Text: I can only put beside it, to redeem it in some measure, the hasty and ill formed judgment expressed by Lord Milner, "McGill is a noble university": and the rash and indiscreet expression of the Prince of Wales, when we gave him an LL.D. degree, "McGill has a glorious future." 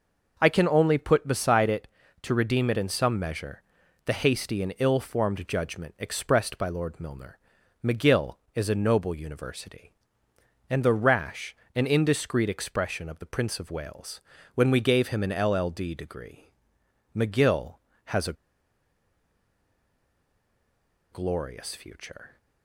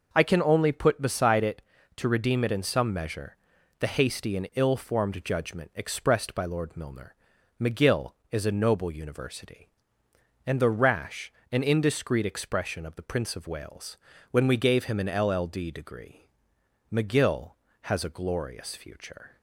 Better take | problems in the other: second | pauses between "a" and "glorious"; strong; at 18.3 s; 2.7 s long

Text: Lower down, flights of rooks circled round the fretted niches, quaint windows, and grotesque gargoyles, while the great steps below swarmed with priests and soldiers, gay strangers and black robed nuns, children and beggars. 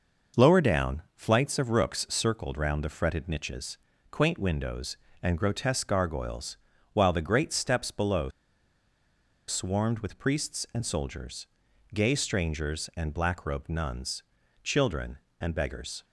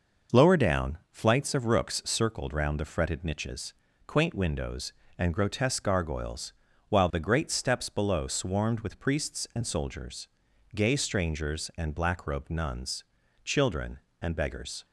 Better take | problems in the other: second | pauses between "below" and "swarmed"; at 8.2 s; 1.1 s long

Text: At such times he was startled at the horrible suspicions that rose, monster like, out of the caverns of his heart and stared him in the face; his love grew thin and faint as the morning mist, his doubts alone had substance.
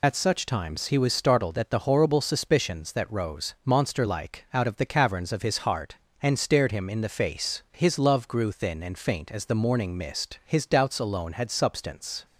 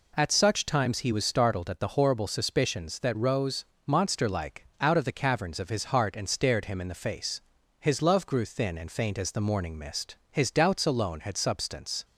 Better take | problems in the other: second | loses the start of "At"; at 0.0 s; 70 ms

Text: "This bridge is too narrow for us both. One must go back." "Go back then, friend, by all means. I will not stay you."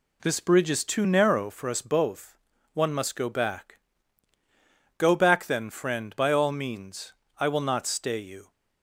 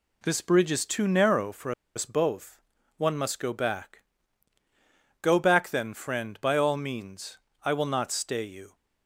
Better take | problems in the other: first | pauses between "for" and "us"; slight; at 1.7 s; 0.24 s long

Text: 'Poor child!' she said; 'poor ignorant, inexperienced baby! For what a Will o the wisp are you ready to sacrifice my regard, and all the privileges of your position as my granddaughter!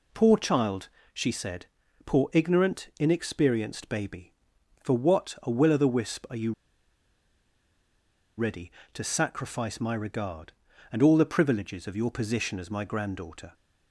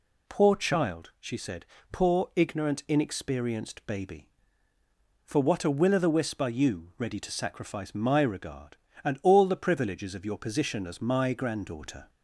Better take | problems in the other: second | pauses between "you" and "ready"; strong; at 6.5 s; 1.8 s long

